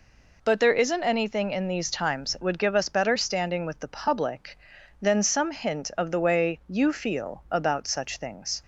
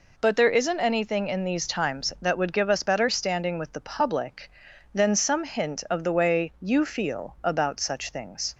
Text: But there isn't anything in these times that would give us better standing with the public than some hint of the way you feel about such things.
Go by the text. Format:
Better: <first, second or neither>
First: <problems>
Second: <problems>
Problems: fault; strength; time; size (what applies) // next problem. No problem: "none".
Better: second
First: skips "that"; at 2.3 s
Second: none